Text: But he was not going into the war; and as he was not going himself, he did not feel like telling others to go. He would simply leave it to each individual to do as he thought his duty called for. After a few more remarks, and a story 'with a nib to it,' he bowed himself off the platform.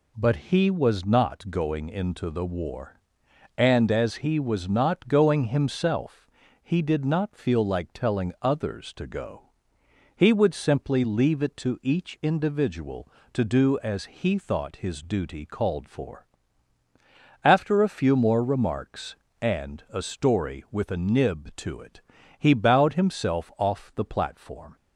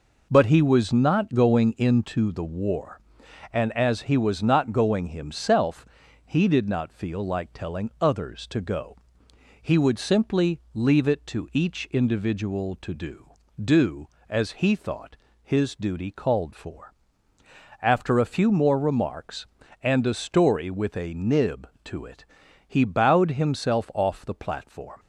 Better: first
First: none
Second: pauses between "simply" and "leave"; slight; at 10.5 s; 0.16 s long // says "do" twice; at 13.6 s // pauses between "thought" and "his"; slight; at 15.1 s; 0.26 s long

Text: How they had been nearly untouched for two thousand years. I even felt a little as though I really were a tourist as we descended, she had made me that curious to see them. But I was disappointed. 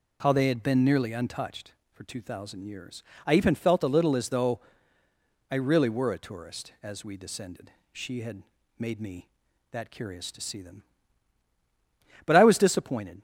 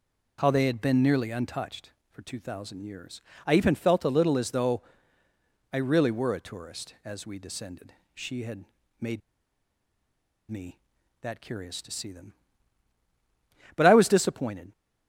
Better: first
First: pauses between "though" and "I"; noticeable; at 4.5 s; 0.94 s long // pauses between "had" and "made"; at 8.4 s; 0.38 s long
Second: pauses between "though" and "I"; noticeable; at 4.7 s; 0.94 s long // pauses between "had" and "made"; at 8.6 s; 0.38 s long // pauses between "made" and "me"; strong; at 9.2 s; 1.2 s long

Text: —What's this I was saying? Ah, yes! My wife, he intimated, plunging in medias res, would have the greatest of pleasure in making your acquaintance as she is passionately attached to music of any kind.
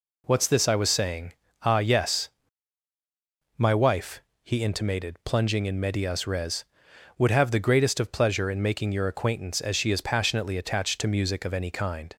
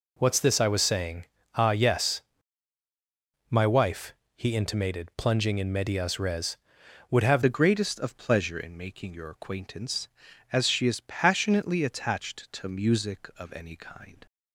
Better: first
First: none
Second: changes voice at "the"; from 7.4 s on; 6.8 s long

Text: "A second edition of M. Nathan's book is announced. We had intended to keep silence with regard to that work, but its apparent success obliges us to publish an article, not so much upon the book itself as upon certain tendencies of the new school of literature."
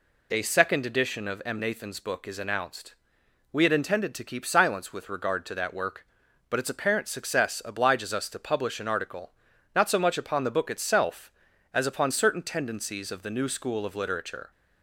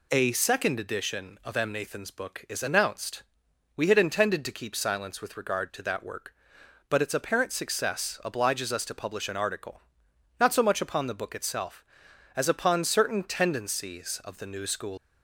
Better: first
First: none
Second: stops before "of literature"; at 14.9 s

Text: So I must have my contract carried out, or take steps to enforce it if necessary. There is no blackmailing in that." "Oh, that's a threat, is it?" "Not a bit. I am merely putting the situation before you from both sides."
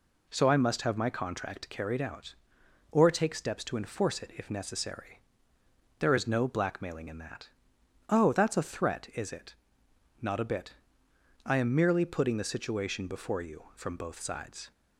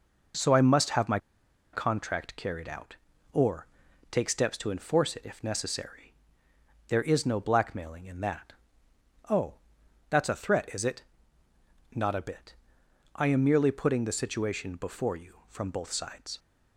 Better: first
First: none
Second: pauses between "my" and "contract"; noticeable; at 1.1 s; 0.55 s long // pauses between "or" and "take"; at 3.6 s; 0.44 s long

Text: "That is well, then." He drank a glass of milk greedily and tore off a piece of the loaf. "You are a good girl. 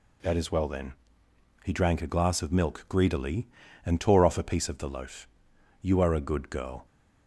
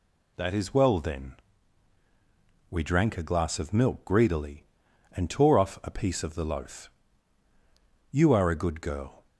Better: first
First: none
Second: says "We" for "He"; at 2.6 s

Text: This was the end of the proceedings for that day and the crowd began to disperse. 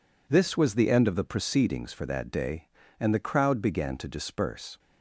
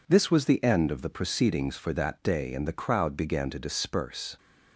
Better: neither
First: none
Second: none

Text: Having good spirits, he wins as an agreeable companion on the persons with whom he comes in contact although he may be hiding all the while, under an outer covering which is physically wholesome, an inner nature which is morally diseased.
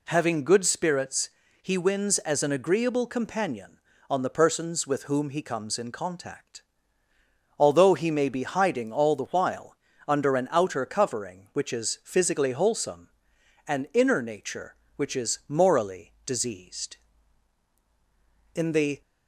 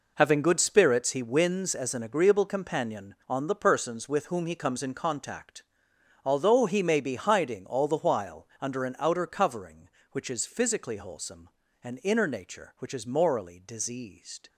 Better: second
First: pauses between "contact" and "although"; noticeable; at 6.6 s; 0.96 s long // pauses between "morally" and "diseased"; slight; at 16.1 s; 0.16 s long // goes on to say "In the"; slight; from 18.5 s on; 0.48 s long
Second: pauses between "contact" and "although"; noticeable; at 5.6 s; 0.62 s long

